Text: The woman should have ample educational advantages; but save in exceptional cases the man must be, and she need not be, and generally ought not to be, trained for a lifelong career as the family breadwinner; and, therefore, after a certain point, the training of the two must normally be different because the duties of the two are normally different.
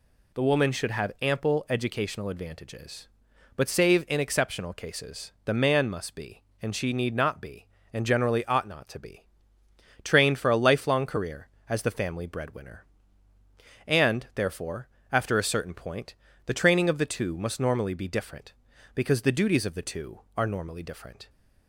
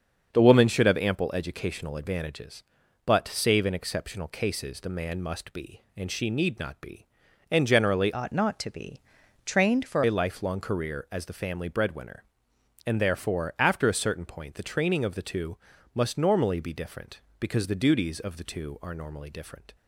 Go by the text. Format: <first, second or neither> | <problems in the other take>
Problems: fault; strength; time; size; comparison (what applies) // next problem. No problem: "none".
first | starts louder than the rest; until 1.3 s; 7 dB // changes voice from "ought" to "for"; from 8.1 to 10.0 s; 1.9 s long // pauses between "two" and "must"; slight; at 15.5 s; 0.36 s long